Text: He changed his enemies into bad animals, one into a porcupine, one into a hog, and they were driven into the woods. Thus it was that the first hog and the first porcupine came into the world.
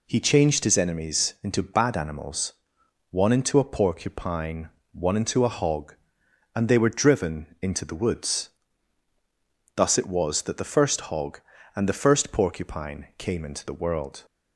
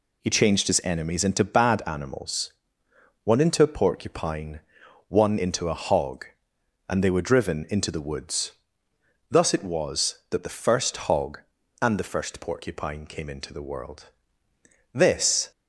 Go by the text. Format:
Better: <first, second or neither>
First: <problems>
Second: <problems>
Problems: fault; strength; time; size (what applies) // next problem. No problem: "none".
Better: first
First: none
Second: goes on to say "This"; from 14.9 s on; 0.58 s long